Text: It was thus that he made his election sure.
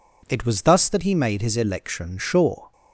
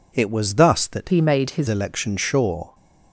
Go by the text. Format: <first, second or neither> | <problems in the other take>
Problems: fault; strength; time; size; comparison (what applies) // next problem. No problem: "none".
first | changes voice from "he" to "his"; from 1.0 to 1.6 s; 0.6 s long